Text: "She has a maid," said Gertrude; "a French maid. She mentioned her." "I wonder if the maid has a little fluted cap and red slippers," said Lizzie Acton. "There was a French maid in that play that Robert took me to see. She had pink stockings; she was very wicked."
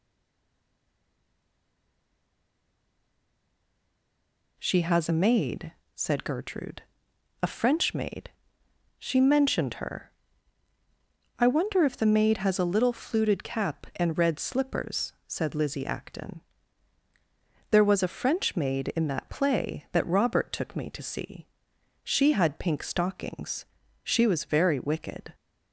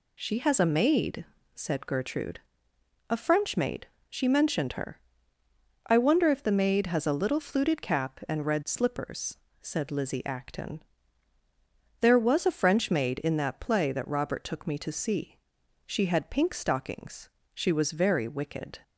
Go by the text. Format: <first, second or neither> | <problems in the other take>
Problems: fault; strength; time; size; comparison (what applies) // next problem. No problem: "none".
second | stays silent before the first word; strong; until 4.5 s; 4.5 s long